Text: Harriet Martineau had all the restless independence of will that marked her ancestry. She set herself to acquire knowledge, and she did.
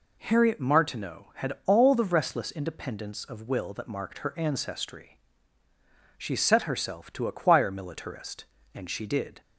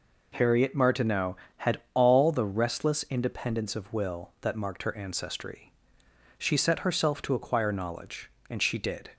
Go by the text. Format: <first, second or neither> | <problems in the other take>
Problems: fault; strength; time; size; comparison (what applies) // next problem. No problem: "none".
second | says "militarist" for "knowledge"; at 7.7 s